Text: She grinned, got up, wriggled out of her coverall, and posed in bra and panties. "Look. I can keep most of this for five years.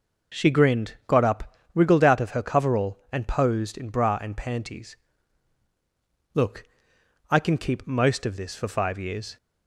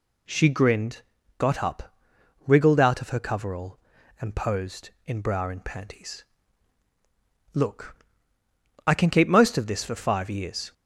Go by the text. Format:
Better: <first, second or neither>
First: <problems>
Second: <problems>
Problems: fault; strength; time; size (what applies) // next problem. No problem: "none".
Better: neither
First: none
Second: none